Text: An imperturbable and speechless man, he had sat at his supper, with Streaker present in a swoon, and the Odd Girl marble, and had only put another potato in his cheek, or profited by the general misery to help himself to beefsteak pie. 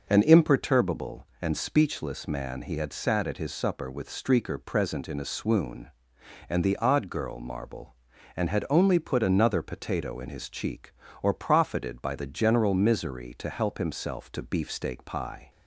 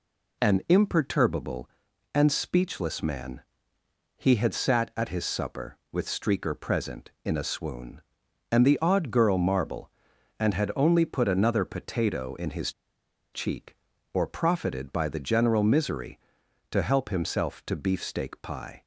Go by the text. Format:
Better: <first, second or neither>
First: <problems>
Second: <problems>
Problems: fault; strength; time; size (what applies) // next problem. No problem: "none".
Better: first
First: none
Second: pauses between "his" and "cheek"; noticeable; at 12.7 s; 0.62 s long